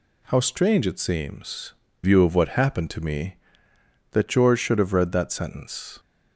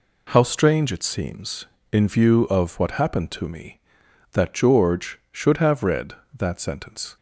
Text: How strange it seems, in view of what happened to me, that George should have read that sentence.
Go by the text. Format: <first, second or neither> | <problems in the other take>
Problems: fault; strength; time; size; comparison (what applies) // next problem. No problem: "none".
second | skips "in"; at 1.8 s